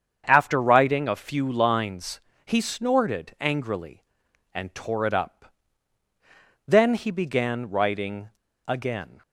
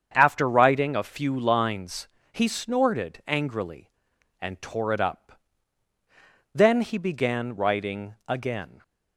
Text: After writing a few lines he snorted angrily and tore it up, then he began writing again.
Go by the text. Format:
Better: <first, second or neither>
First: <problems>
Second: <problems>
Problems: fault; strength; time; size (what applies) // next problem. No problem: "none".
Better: second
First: starts louder than the rest; strong; until 1.2 s; 7.5 dB // pauses between "lines" and "he"; slight; at 2.1 s; 0.28 s long // pauses between "writing" and "again"; slight; at 8.3 s; 0.35 s long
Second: starts louder than the rest; strong; until 1.1 s; 7.5 dB // pauses between "lines" and "he"; slight; at 2.0 s; 0.27 s long